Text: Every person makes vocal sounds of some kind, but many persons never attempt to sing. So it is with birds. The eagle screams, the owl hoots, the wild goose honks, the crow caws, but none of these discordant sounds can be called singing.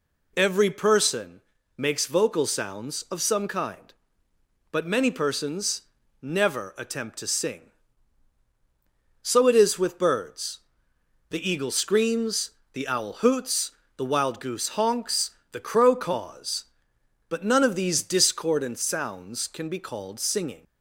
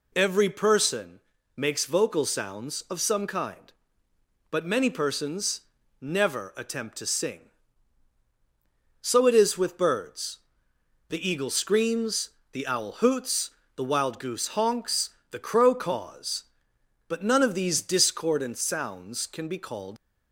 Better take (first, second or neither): first